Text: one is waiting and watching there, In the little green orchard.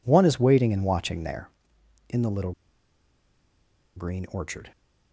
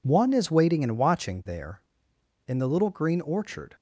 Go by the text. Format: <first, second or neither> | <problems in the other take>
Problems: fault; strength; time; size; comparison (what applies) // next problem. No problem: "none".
second | pauses between "little" and "green"; strong; at 2.5 s; 1.4 s long